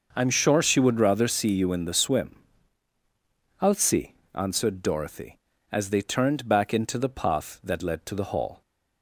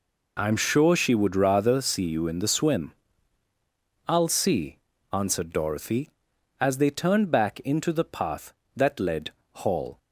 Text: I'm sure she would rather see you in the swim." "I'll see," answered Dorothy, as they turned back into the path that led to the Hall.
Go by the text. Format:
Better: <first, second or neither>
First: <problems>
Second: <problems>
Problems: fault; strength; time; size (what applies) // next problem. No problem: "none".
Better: first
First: none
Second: skips "to the"; at 9.4 s